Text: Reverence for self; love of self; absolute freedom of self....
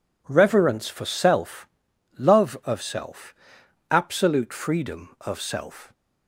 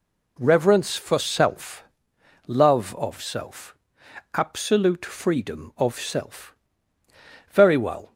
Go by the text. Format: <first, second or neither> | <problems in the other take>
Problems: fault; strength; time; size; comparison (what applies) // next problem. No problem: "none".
first | goes on to say "Very well"; noticeable; from 7.5 s on; 0.62 s long